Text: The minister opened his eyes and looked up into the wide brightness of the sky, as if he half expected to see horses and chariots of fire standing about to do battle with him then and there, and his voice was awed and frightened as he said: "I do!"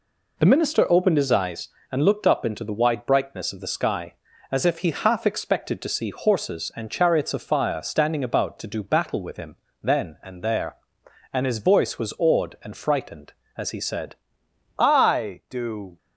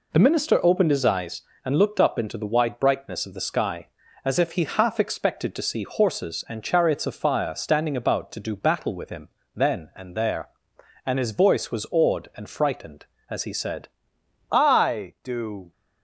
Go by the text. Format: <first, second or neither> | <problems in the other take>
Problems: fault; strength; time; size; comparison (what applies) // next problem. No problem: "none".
neither | pauses between "him" and "then"; slight; the same in both